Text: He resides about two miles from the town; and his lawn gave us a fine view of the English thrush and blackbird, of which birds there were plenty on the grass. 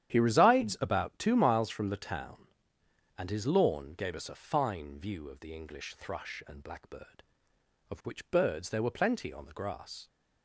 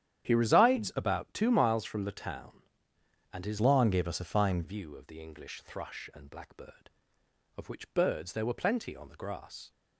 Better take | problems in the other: first | starts louder than the rest; strong; until 1.3 s; 10 dB; strong in the first // changes voice from "lawn" to "fine"; from 3.5 to 4.6 s; 1.1 s long

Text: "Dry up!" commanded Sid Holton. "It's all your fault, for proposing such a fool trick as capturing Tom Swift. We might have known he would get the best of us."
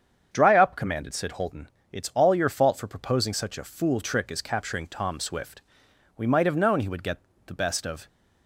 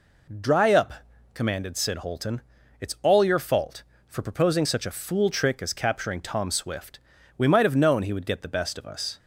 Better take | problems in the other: second | starts louder than the rest; strong; until 1.3 s; 7.5 dB // pauses between "get" and "the"; slight; at 7.1 s; 0.30 s long // stops before "us"; at 8.0 s

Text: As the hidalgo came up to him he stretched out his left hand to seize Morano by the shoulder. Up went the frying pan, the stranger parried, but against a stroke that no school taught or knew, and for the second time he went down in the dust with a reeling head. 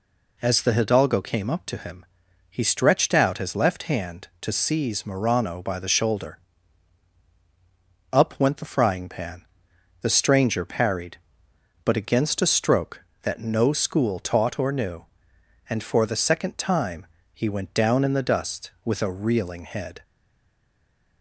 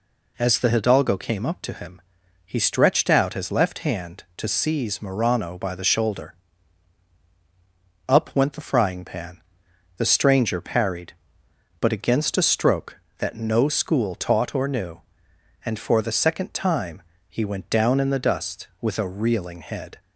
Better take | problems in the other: second | pauses between "him" and "he"; at 2.0 s; 0.42 s long; also in the second // pauses between "time" and "he"; slight; at 17.0 s; 0.26 s long; slight in the second // stays silent after the last word; noticeable; from 20.0 s on; 1.2 s long

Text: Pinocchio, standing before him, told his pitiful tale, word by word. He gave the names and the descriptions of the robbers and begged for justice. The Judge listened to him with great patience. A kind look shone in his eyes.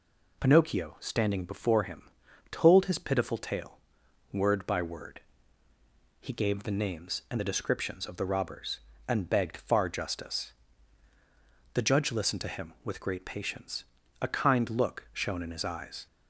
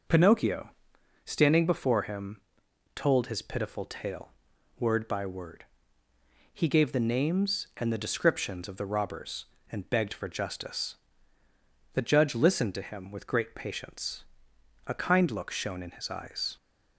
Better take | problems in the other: second | says "far" for "for"; at 9.5 s

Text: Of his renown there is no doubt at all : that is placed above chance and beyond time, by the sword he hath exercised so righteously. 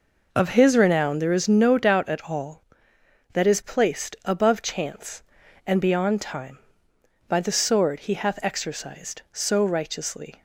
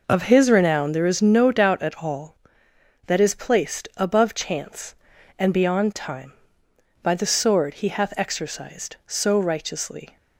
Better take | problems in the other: neither | none

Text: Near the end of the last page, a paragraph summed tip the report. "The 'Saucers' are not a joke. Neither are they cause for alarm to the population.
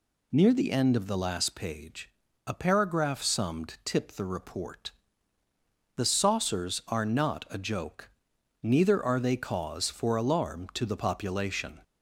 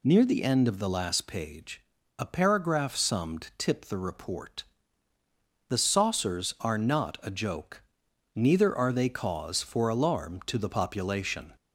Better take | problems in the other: neither | none

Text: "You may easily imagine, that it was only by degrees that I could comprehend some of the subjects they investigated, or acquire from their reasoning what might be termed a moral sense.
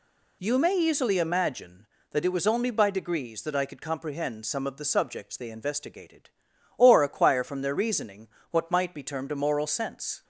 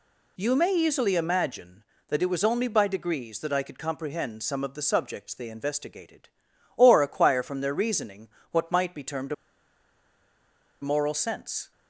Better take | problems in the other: first | pauses between "reasoning" and "what"; slight; at 8.2 s; 0.24 s long; slight in the first // pauses between "a" and "moral"; strong; at 9.3 s; 1.4 s long

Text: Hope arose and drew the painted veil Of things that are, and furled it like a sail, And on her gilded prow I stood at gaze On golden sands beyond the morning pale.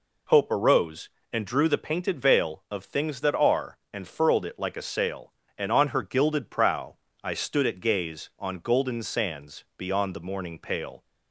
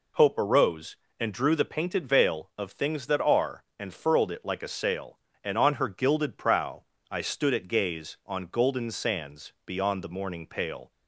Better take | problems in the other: neither | pauses between "prow" and "I"; slight; the same in both

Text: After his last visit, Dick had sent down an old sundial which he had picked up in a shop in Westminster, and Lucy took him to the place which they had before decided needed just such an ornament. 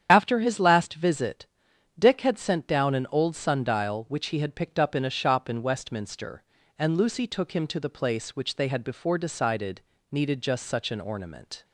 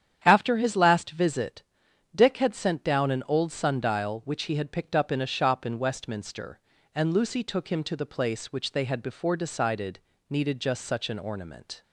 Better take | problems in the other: second | loses the start of "After"; at 0.0 s; 40 ms // starts louder than the rest; strong; until 1.1 s; 9 dB; strong in the second // pauses between "decided" and "needed"; slight; at 9.7 s; 0.32 s long; slight in the second

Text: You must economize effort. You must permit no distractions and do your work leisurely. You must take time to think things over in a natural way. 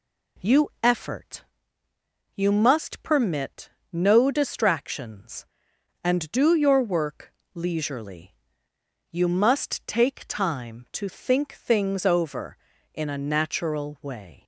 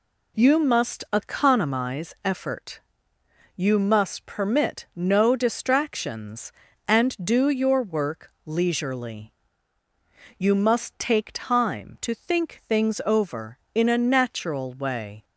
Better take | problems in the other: second | skips "must economize"; at 0.7 s // pauses between "permit" and "no"; slight; at 3.6 s; 0.22 s long // pauses between "work" and "leisurely"; slight; at 7.3 s; 0.24 s long

